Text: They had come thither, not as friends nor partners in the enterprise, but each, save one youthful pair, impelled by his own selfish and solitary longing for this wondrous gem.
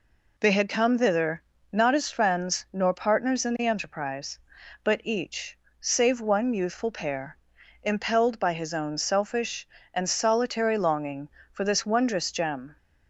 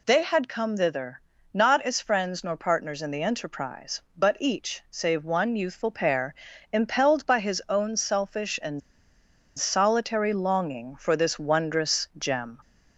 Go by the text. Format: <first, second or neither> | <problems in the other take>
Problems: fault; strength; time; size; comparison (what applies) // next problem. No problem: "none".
first | pauses between "and" and "solitary"; noticeable; at 8.8 s; 0.77 s long